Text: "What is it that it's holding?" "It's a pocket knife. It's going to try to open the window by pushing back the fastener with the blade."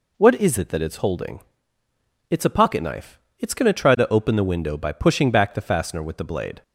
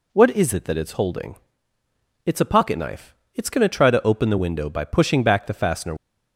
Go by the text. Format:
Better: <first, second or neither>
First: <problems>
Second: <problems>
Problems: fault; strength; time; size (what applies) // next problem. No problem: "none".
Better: first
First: none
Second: stops before "with the blade"; at 5.9 s